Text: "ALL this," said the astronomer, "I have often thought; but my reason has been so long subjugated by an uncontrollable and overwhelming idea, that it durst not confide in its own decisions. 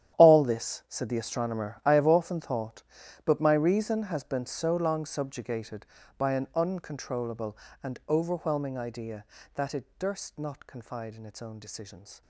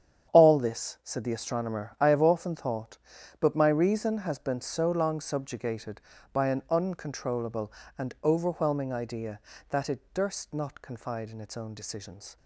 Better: second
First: gets quieter; strong; throughout; 15 dB // starts louder than the rest; strong; until 1.2 s; 10.5 dB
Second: starts louder than the rest; strong; until 1.3 s; 8.5 dB

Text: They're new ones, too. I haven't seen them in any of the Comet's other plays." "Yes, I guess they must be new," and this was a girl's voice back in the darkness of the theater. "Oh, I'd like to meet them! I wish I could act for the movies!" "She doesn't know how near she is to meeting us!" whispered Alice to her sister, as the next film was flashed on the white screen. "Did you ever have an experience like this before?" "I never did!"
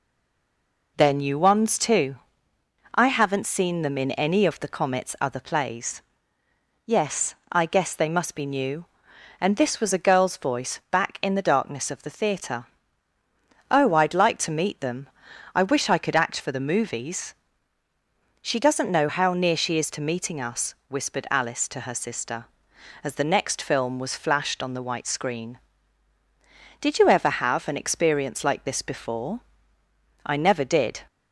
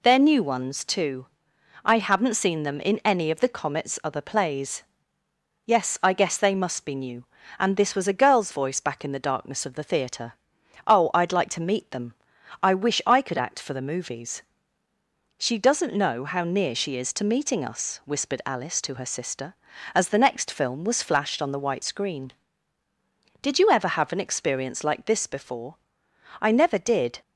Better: second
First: stays silent before the first word; slight; until 0.9 s; 0.9 s long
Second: none

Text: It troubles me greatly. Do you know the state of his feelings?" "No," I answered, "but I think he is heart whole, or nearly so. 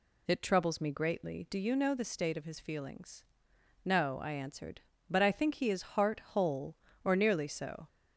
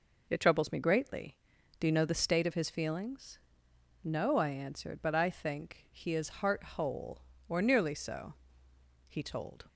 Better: first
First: none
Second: goes on to say "He told"; from 9.0 s on; 0.60 s long

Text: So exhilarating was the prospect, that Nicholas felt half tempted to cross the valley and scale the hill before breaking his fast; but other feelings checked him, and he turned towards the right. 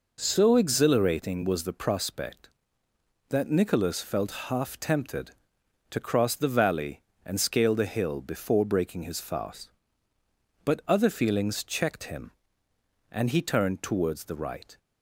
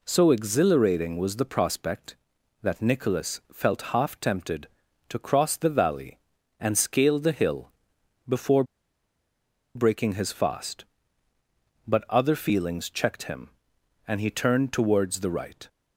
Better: first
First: none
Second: pauses between "hill" and "before"; noticeable; at 7.7 s; 0.56 s long // pauses between "before" and "breaking"; at 8.6 s; 1.1 s long

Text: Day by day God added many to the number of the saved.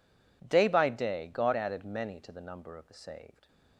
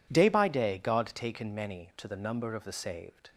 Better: first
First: none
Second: says "taken" for "added"; at 1.1 s

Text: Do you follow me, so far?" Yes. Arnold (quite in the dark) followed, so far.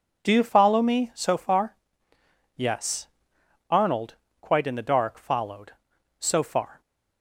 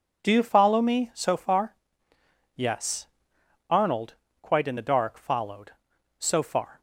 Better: neither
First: none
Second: none

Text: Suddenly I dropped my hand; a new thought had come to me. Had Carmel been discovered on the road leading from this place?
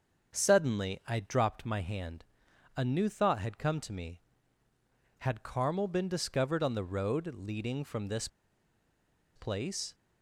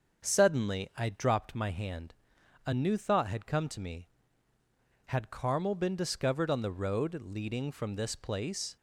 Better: second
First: starts louder than the rest; until 1.3 s; 6.5 dB // pauses between "this" and "place"; at 8.2 s; 1.0 s long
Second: starts louder than the rest; until 1.2 s; 6.5 dB

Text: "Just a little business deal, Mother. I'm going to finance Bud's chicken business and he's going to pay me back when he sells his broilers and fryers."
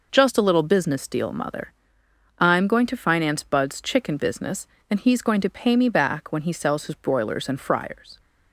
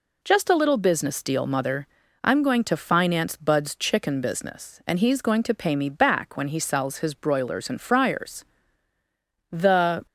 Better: first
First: none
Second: goes on to say "The"; from 9.5 s on; 0.54 s long

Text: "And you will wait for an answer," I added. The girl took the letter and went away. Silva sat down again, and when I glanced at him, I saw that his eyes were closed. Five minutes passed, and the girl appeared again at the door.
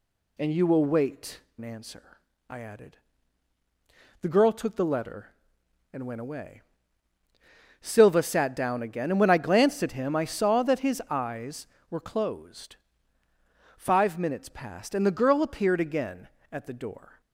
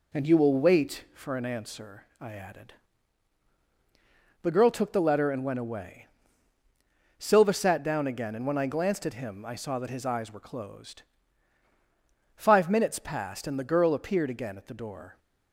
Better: second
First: skips "for"; at 1.4 s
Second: none

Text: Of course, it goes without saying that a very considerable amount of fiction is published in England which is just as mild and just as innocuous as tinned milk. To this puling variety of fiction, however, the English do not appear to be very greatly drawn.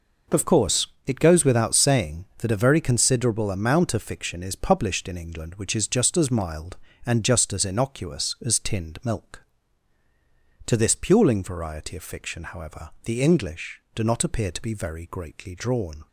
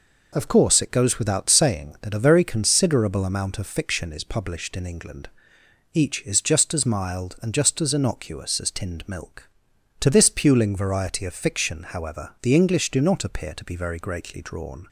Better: first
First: none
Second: says "each" for "which"; at 5.9 s

